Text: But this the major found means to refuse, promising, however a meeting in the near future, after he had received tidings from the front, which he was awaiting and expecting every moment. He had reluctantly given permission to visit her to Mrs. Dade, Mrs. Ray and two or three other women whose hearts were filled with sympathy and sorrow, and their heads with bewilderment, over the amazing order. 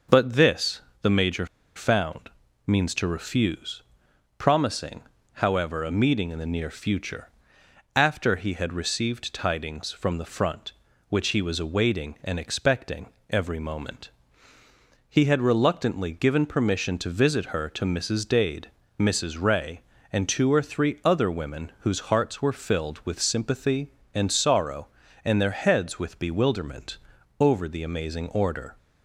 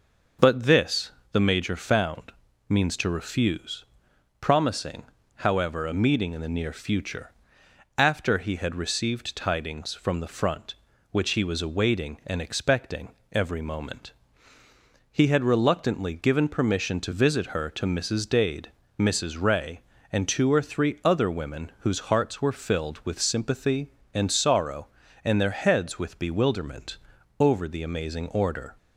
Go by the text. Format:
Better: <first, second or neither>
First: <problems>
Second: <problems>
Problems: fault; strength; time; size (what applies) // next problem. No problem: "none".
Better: second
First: starts louder than the rest; noticeable; until 1.3 s; 6 dB // pauses between "this" and "the"; slight; at 0.8 s; 0.20 s long // pauses between "major" and "found"; slight; at 1.4 s; 0.30 s long // pauses between "found" and "means"; at 2.2 s; 0.38 s long // pauses between "expecting" and "every"; slight; at 13.0 s; 0.24 s long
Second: pauses between "this" and "the"; slight; at 1.1 s; 0.20 s long // pauses between "found" and "means"; at 2.3 s; 0.38 s long // pauses between "expecting" and "every"; slight; at 13.0 s; 0.24 s long